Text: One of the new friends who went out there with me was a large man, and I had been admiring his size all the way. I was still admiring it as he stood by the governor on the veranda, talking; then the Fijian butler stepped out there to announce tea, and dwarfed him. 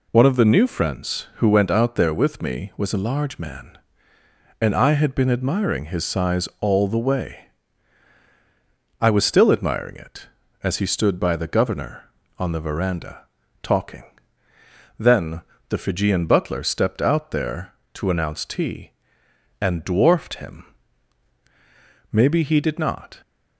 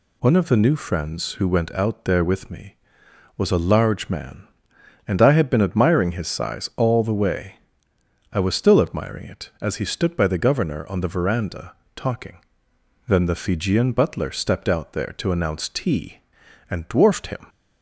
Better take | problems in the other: second | pauses between "then" and "the"; slight; at 15.4 s; 0.26 s long // goes on to say "Maybe he did not"; noticeable; from 22.1 s on; 1.1 s long

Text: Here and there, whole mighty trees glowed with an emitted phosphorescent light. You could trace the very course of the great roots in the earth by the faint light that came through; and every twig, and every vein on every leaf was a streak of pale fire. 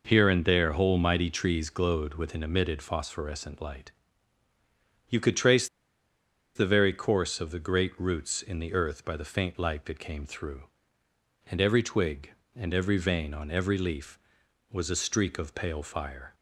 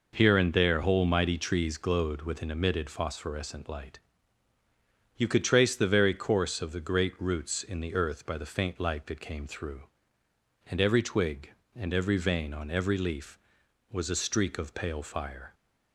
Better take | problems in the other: second | pauses between "trace" and "the"; noticeable; at 5.6 s; 0.89 s long

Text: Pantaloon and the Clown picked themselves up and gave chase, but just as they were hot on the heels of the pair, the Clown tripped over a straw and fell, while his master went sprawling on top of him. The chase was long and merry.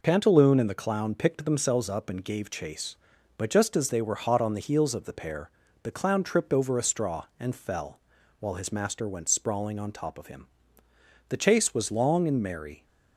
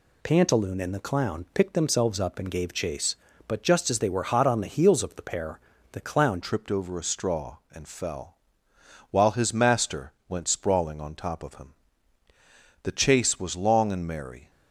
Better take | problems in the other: first | changes voice at "tripped"; from 6.4 s on; 8.0 s long // pauses between "master" and "went"; slight; at 10.1 s; 0.16 s long

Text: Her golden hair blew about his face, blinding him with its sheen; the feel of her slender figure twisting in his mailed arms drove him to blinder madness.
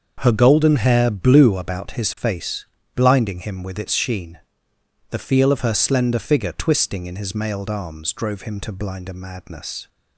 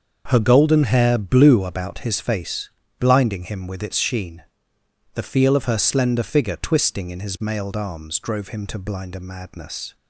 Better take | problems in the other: neither | starts louder than the rest; the same in both

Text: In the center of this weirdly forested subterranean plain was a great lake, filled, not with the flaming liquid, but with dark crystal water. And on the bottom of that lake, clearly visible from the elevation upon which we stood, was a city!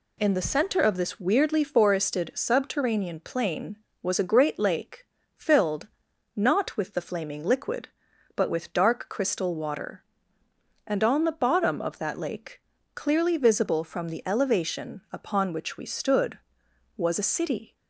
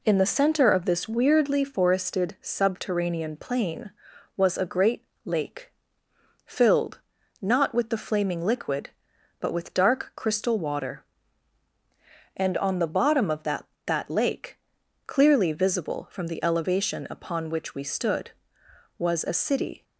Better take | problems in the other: first | pauses between "great" and "lake"; slight; at 5.0 s; 0.22 s long // says "that" twice; at 13.8 s

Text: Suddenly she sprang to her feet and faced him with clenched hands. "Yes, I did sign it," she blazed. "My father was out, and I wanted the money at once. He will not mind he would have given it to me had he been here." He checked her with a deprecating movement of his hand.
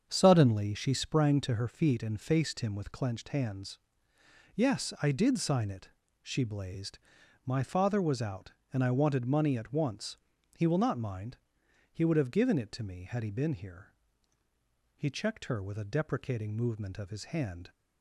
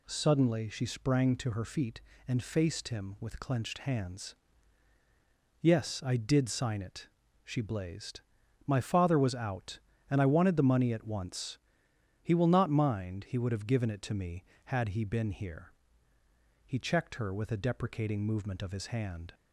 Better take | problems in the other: second | starts louder than the rest; strong; until 1.1 s; 7 dB // skips "the"; at 9.2 s // pauses between "mind" and "he"; noticeable; at 11.3 s; 0.54 s long

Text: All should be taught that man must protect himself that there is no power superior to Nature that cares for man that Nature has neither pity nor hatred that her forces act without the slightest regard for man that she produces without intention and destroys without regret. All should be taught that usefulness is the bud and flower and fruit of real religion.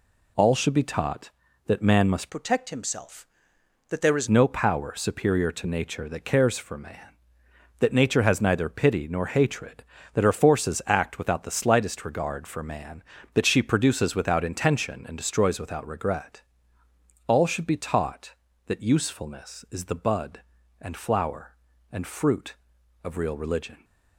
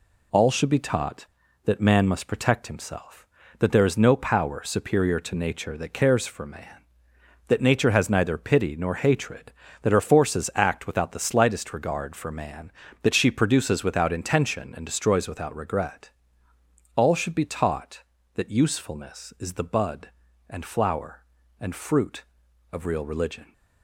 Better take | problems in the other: second | changes voice from "protect" to "is"; from 2.2 to 4.2 s; 2.0 s long

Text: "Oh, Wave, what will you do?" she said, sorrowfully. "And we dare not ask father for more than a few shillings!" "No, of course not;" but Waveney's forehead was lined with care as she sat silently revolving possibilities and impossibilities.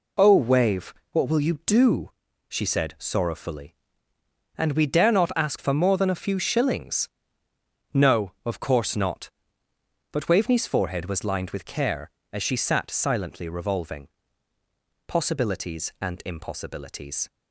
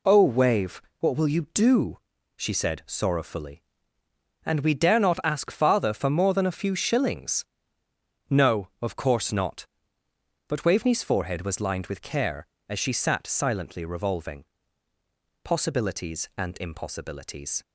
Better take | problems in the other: second | skips "father"; at 5.5 s // pauses between "revolving" and "possibilities"; noticeable; at 14.0 s; 0.98 s long; noticeable in the second

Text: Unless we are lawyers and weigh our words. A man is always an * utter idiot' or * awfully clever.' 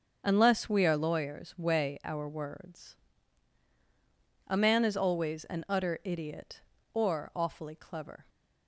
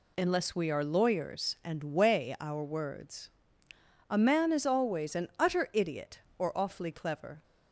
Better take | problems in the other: second | starts louder than the rest; until 1.2 s; 7 dB // skips "and"; at 1.5 s

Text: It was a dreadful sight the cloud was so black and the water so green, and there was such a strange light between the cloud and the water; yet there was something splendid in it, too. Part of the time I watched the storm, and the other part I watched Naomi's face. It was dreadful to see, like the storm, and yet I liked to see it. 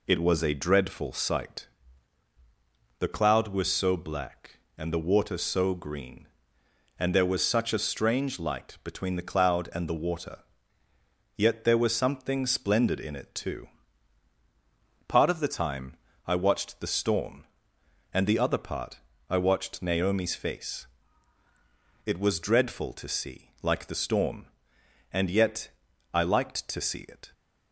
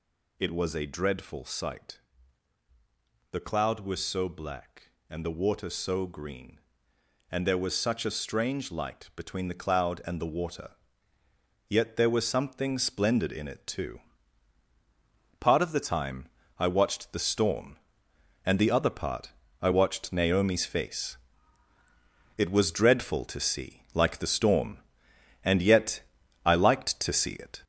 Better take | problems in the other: first | gets louder; noticeable; throughout; 5.5 dB // pauses between "sight" and "the"; strong; at 1.9 s; 1.3 s long; strong in the first // pauses between "time" and "I"; slight; at 16.2 s; 0.30 s long; slight in the first // pauses between "part" and "I"; slight; at 19.3 s; 0.32 s long; slight in the first // pauses between "yet" and "I"; at 26.0 s; 0.44 s long; also in the first

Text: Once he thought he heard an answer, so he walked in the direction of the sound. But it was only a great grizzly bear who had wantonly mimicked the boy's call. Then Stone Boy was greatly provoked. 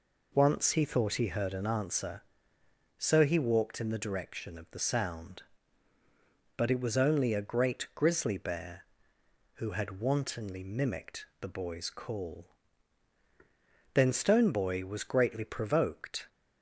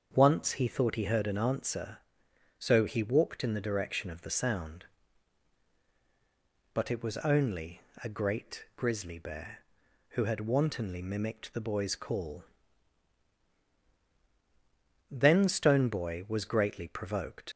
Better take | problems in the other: first | starts louder than the rest; until 1.1 s; 7 dB // pauses between "only" and "a"; slight; at 7.7 s; 0.24 s long // leaves "provoked" unfinished; at 17.5 s; 100 ms

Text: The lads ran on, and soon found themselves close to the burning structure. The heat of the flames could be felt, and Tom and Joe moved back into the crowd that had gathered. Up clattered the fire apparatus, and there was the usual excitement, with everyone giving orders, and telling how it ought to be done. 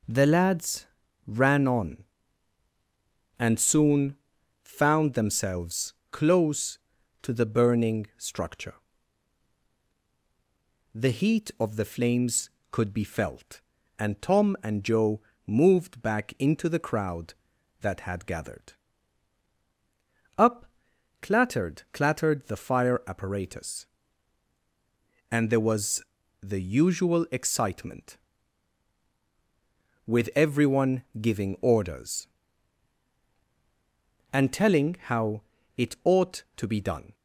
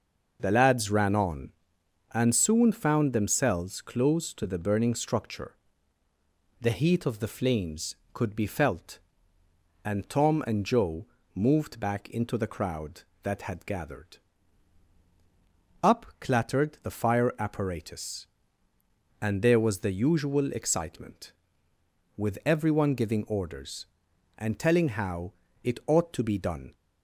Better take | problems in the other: second | pauses between "lads" and "ran"; at 0.8 s; 0.42 s long // pauses between "soon" and "found"; noticeable; at 4.1 s; 0.46 s long // pauses between "themselves" and "close"; slight; at 5.9 s; 0.16 s long // pauses between "Joe" and "moved"; slight; at 15.2 s; 0.24 s long; slight in the second // pauses between "Up" and "clattered"; noticeable; at 20.6 s; 0.56 s long // says "clattered" twice; at 21.9 s // pauses between "was" and "the"; at 26.0 s; 0.40 s long // pauses between "everyone" and "giving"; slight; at 31.0 s; 0.16 s long // pauses between "how" and "it"; at 35.4 s; 0.38 s long; slight in the second

